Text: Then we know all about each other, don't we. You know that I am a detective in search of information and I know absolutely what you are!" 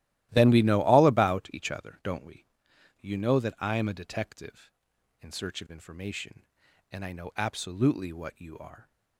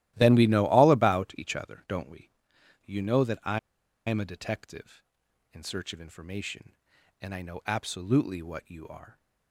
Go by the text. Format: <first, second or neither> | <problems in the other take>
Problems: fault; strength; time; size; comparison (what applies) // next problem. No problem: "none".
first | starts louder than the rest; strong; until 1.1 s; 15 dB; strong in the first // pauses between "I" and "am"; noticeable; at 3.5 s; 0.49 s long